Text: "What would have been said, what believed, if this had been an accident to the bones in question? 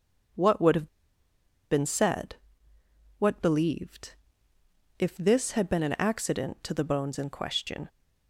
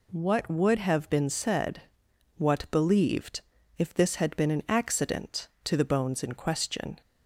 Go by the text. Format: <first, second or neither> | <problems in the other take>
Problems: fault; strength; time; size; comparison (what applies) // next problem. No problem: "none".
second | starts louder than the rest; until 2.2 s; 6.5 dB // pauses between "have" and "been"; noticeable; at 0.8 s; 0.84 s long